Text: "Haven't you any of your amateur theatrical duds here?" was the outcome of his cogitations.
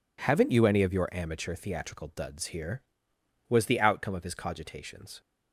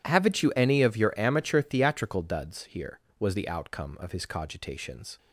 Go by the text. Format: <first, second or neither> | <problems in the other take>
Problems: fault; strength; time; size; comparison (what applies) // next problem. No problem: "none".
neither | none